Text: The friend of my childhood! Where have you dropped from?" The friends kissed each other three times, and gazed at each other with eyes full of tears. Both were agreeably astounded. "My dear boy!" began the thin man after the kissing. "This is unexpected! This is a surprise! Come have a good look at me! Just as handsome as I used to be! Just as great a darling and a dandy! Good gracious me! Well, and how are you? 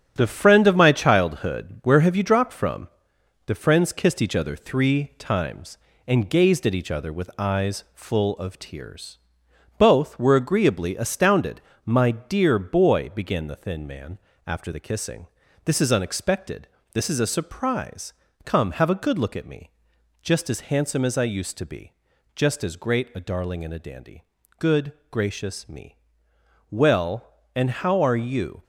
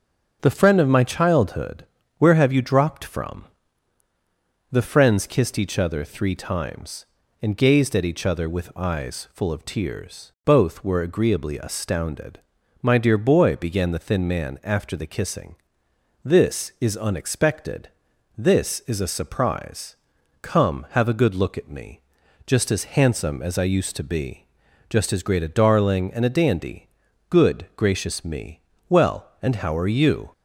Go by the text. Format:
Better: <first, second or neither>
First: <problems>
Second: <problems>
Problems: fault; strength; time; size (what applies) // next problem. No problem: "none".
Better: second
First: gets quieter; noticeable; throughout; 6 dB // starts louder than the rest; strong; until 1.1 s; 8.5 dB // pauses between "man" and "after"; slight; at 14.1 s; 0.30 s long // pauses between "Good" and "gracious"; slight; at 24.9 s; 0.18 s long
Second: starts louder than the rest; until 1.4 s; 6.5 dB